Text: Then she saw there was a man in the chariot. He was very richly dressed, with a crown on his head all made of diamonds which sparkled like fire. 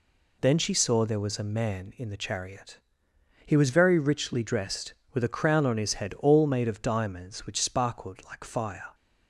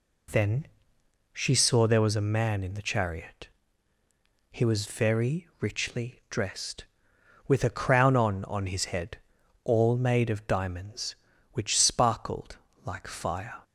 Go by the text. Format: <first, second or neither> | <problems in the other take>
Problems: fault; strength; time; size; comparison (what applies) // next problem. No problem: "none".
first | pauses between "Then" and "she"; noticeable; at 0.6 s; 0.66 s long // says "on" twice; at 8.4 s // pauses between "head" and "all"; noticeable; at 9.1 s; 0.46 s long // pauses between "sparkled" and "like"; slight; at 12.5 s; 0.28 s long